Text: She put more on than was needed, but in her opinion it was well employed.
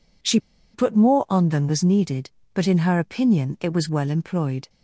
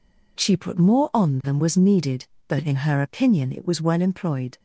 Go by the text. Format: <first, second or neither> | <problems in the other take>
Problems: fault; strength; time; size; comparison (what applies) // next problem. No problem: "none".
second | pauses between "She" and "put"; slight; at 0.3 s; 0.35 s long